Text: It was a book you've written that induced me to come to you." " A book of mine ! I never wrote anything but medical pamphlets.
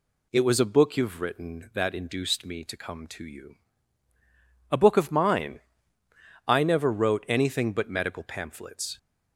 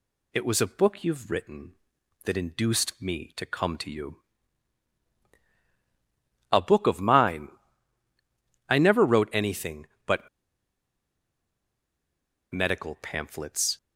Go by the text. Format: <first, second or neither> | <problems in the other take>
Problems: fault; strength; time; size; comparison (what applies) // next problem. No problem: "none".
first | pauses between "but" and "medical"; strong; at 10.2 s; 2.2 s long